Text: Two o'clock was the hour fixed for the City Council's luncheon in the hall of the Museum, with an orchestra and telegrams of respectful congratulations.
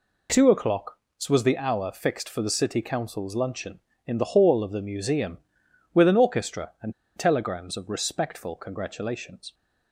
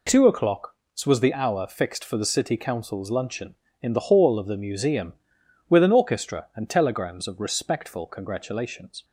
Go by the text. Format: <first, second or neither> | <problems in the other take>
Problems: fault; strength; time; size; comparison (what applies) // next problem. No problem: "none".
second | pauses between "and" and "telegrams"; slight; at 6.9 s; 0.24 s long